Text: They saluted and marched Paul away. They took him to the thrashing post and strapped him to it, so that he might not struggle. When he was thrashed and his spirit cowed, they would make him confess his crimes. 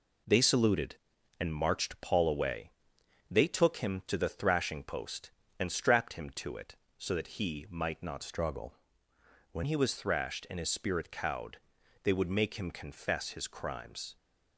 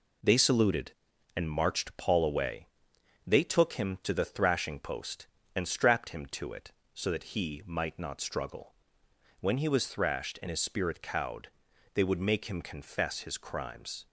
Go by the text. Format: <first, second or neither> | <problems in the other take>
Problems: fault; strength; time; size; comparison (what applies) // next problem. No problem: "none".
second | changes voice from "struggle" to "When"; from 8.2 to 9.6 s; 1.4 s long